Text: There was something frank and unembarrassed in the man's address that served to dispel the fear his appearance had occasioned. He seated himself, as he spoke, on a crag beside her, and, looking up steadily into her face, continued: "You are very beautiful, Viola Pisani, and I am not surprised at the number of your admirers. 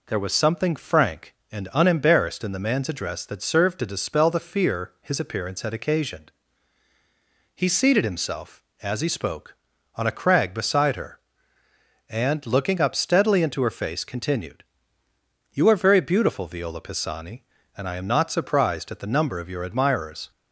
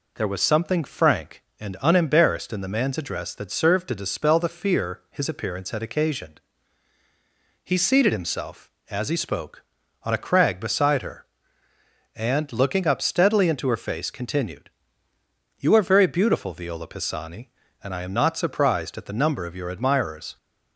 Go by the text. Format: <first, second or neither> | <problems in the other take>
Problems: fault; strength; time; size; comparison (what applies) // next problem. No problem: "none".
neither | none